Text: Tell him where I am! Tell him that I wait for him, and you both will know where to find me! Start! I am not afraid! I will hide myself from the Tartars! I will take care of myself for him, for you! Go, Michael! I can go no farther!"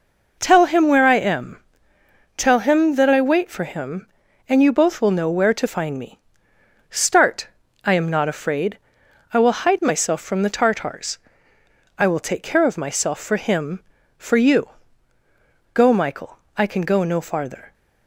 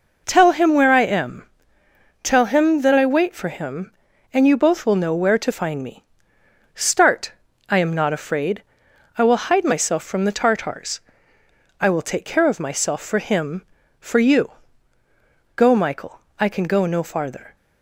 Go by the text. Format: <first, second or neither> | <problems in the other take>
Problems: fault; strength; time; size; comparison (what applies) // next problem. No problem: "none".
neither | none